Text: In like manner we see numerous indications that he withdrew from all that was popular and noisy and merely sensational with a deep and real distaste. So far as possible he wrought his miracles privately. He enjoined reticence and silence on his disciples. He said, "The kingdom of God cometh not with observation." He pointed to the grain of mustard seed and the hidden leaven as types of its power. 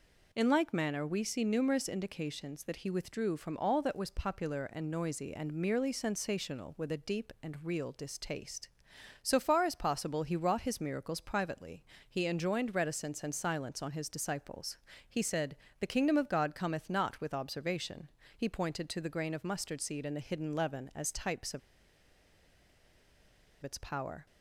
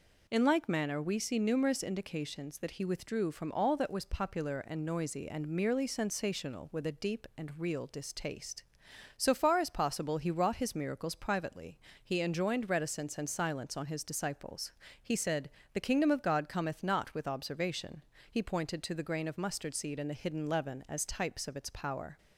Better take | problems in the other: second | pauses between "of" and "its"; strong; at 21.6 s; 2.0 s long

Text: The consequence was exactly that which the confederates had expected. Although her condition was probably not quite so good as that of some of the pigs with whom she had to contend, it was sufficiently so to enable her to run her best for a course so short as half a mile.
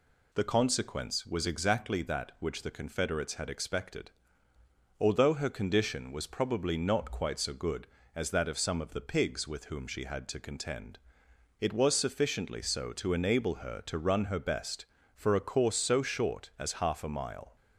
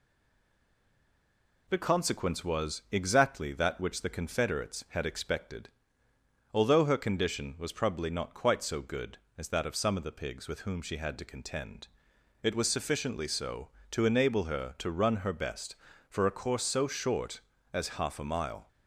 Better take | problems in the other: first | stays silent before the first word; noticeable; until 1.6 s; 1.6 s long

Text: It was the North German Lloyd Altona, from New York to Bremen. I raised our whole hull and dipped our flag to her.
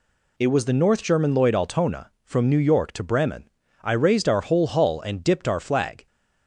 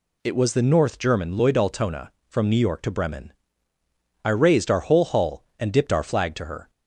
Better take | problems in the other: second | stops before "to her"; at 6.0 s

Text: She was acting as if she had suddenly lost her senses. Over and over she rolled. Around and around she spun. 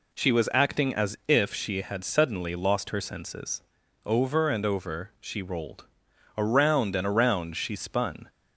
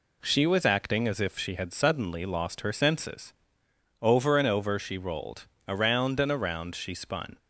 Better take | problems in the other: neither | none

